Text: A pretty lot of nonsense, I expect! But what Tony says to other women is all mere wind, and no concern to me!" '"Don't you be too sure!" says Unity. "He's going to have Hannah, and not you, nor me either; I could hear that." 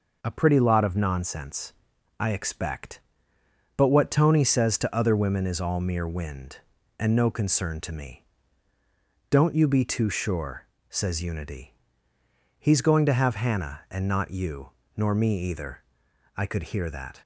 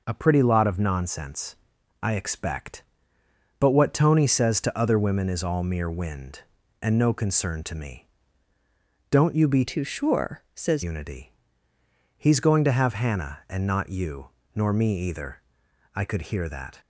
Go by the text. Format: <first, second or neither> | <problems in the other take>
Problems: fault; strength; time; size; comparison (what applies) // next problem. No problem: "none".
first | changes voice from "too" to "says"; from 9.6 to 10.8 s; 1.2 s long